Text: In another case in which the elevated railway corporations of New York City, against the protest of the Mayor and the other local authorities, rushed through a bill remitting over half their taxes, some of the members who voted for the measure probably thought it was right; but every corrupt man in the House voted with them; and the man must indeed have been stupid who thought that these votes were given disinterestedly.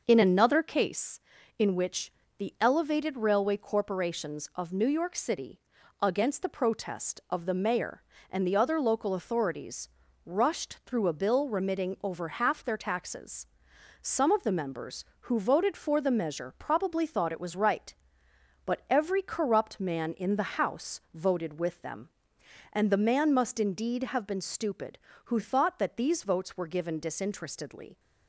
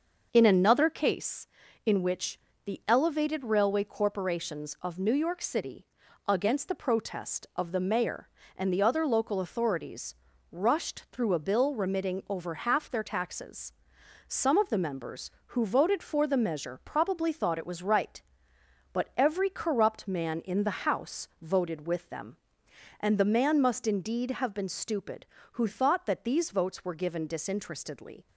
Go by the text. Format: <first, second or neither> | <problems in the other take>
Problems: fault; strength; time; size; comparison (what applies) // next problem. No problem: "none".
neither | pauses between "which" and "the"; slight; the same in both